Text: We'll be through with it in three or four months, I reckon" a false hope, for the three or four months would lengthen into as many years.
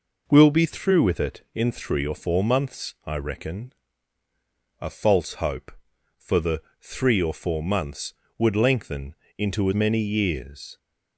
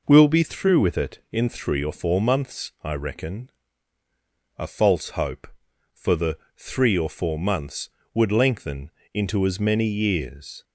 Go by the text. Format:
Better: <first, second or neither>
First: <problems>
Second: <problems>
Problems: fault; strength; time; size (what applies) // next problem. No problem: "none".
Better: second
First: pauses between "reckon" and "a"; at 3.7 s; 1.1 s long // pauses between "the" and "three"; slight; at 6.6 s; 0.20 s long // pauses between "lengthen" and "into"; slight; at 9.1 s; 0.24 s long // skips "as"; at 9.7 s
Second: pauses between "reckon" and "a"; at 3.4 s; 1.1 s long // pauses between "the" and "three"; slight; at 6.3 s; 0.20 s long // pauses between "lengthen" and "into"; slight; at 8.8 s; 0.24 s long